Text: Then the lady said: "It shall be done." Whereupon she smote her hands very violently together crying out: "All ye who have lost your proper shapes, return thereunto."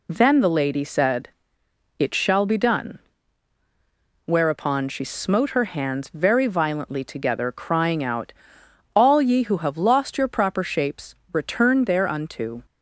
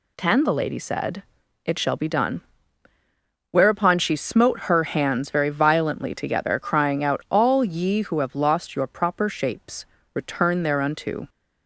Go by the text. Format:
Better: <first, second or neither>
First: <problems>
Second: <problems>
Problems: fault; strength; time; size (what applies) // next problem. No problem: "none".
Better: first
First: none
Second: says "Ten" for "Then"; at 0.1 s